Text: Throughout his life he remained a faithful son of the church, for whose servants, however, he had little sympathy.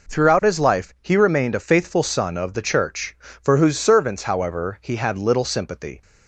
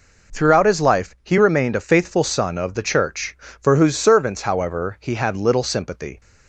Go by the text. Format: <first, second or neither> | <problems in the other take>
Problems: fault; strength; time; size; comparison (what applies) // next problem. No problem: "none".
neither | none